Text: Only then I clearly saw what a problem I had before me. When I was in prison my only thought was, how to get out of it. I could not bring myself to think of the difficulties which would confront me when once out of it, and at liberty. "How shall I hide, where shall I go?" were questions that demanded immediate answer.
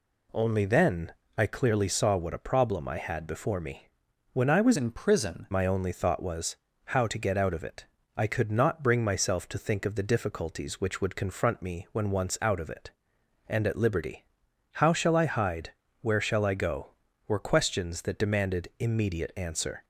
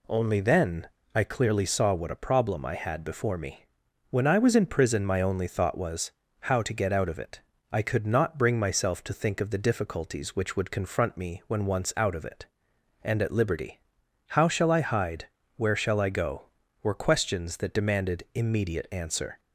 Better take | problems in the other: second | pauses between "then" and "I"; slight; at 1.1 s; 0.22 s long; slight in the second // changes voice from "in" to "prison"; from 4.7 to 5.4 s; 0.7 s long

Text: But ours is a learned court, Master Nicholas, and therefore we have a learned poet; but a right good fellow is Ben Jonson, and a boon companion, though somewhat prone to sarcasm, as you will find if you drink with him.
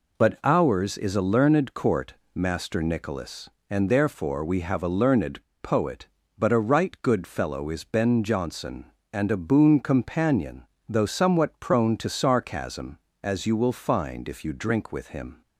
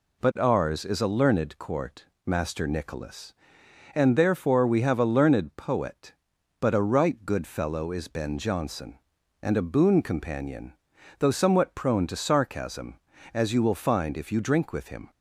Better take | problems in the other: second | pauses between "learned" and "poet"; slight; at 5.4 s; 0.18 s long

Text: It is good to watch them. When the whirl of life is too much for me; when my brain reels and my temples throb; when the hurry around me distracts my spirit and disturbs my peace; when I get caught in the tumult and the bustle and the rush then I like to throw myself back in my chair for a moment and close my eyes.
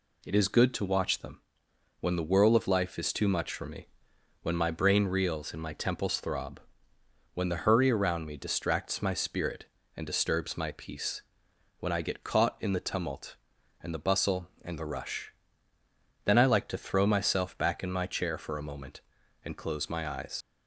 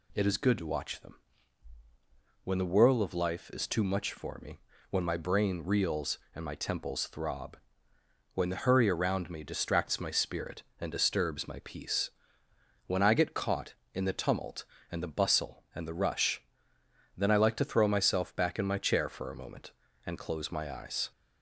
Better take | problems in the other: second | pauses between "rush" and "then"; noticeable; at 15.3 s; 0.94 s long; noticeable in the second // leaves "eyes" unfinished; at 20.4 s; 70 ms

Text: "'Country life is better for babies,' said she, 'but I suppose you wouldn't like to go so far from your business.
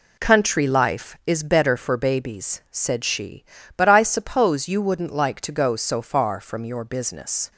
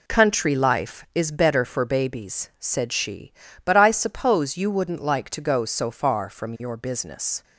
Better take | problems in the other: neither | none

